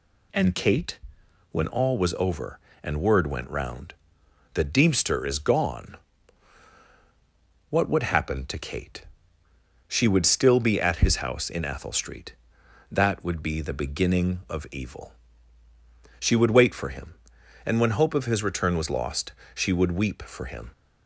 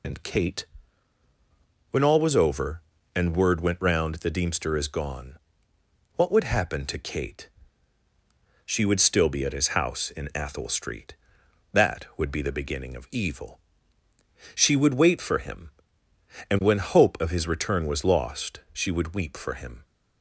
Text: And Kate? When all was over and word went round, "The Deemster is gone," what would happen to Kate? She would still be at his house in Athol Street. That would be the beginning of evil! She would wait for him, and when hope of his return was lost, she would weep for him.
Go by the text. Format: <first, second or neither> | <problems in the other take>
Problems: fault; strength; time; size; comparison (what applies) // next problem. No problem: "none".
first | loses the start of "And"; at 0.0 s; 40 ms